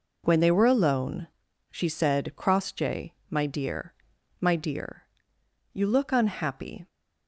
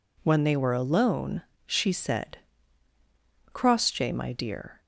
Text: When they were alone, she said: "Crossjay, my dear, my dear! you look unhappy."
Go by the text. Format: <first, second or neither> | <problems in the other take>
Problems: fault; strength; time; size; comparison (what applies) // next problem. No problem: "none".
first | stops before "my dear you look unhappy"; at 4.8 s